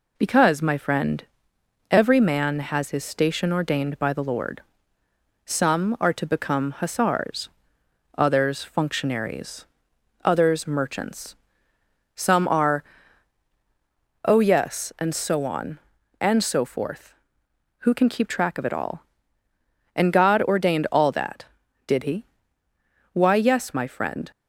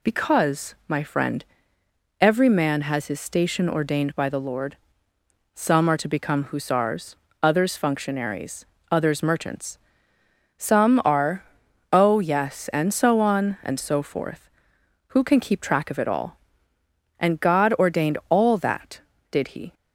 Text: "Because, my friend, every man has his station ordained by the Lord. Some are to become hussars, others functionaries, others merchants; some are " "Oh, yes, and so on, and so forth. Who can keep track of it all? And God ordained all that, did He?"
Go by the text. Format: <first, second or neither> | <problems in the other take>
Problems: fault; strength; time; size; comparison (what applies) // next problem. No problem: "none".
second | goes on to say "Why yes my friend"; noticeable; from 23.1 s on; 1.1 s long